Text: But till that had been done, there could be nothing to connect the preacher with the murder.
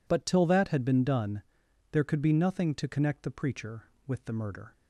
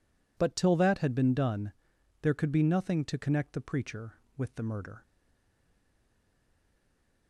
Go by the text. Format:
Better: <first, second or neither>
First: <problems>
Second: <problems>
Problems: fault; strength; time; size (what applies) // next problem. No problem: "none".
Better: first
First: none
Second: stays silent after the last word; from 5.0 s on; 2.2 s long